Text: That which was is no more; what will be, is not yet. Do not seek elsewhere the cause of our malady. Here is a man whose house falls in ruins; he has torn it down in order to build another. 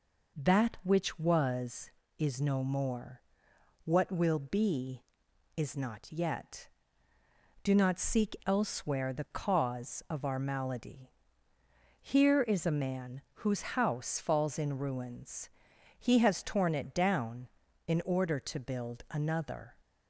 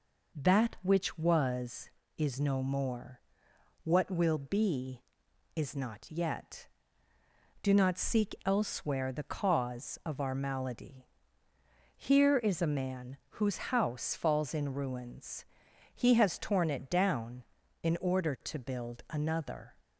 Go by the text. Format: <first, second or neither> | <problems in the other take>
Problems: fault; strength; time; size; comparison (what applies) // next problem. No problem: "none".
neither | none